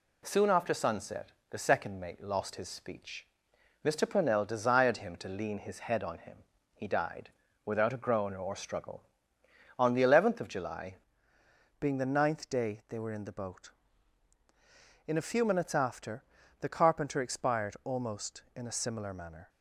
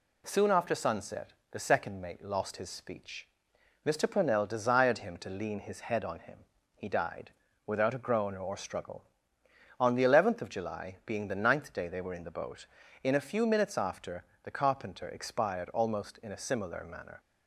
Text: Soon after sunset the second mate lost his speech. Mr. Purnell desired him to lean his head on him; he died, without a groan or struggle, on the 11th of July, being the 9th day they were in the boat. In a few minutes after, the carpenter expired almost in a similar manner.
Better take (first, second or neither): second